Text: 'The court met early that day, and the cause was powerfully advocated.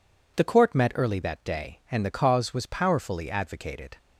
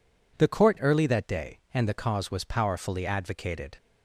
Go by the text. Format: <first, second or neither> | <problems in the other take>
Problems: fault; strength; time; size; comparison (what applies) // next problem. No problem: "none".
first | skips "met"; at 0.7 s